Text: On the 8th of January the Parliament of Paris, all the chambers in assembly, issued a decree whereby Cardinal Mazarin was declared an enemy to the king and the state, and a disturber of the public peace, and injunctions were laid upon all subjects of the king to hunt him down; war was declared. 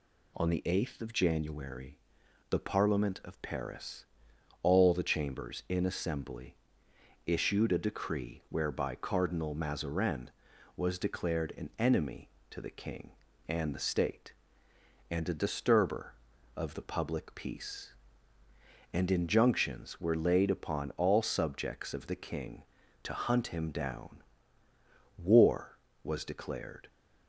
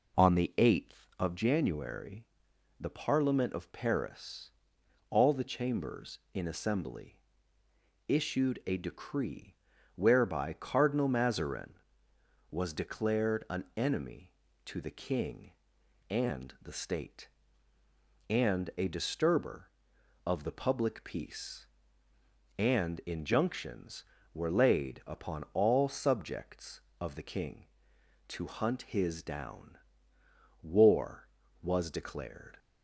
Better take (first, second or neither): first